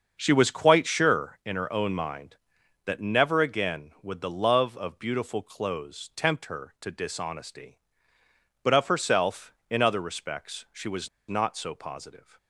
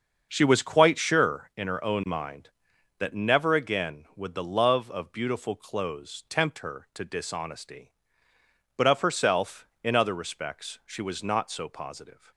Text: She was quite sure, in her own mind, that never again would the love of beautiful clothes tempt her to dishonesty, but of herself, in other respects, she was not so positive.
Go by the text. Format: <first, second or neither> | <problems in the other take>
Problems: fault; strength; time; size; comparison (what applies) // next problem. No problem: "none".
second | starts louder than the rest; until 1.2 s; 6.5 dB; also in the second // pauses between "was" and "not"; slight; at 11.0 s; 0.21 s long